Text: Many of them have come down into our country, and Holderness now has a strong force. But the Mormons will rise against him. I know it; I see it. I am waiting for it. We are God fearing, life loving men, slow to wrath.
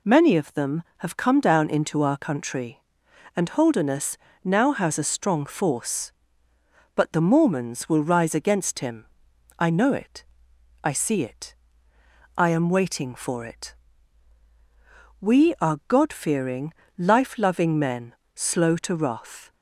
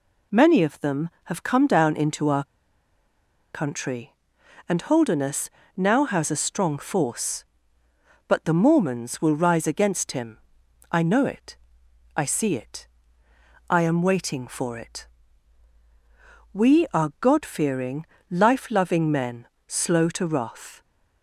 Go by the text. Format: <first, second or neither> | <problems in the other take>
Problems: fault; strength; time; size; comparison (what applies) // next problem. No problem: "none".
first | pauses between "our" and "country"; at 2.4 s; 1.0 s long // pauses between "Holderness" and "now"; slight; at 5.4 s; 0.26 s long; slight in the first